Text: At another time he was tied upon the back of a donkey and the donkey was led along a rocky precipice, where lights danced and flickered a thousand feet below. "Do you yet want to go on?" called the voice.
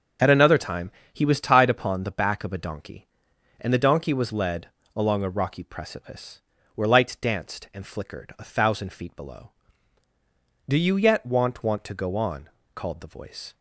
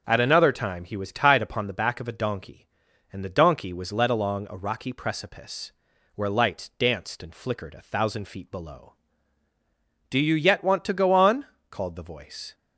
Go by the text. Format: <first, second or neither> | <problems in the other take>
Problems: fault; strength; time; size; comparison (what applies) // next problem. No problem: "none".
second | starts louder than the rest; until 1.4 s; 6.5 dB; also in the second // pauses between "time" and "he"; slight; at 0.9 s; 0.20 s long // pauses between "led" and "along"; slight; at 4.6 s; 0.26 s long // says "want" twice; at 11.6 s